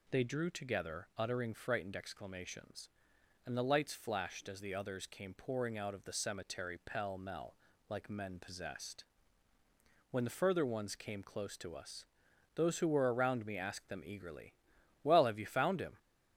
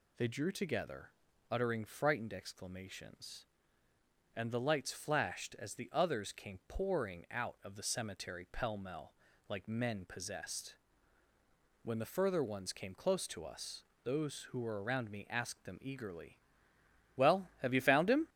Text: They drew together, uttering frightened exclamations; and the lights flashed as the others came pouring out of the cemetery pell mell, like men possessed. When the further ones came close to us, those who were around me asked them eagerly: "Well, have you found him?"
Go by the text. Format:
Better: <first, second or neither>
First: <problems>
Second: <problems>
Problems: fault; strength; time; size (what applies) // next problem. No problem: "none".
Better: neither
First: none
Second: none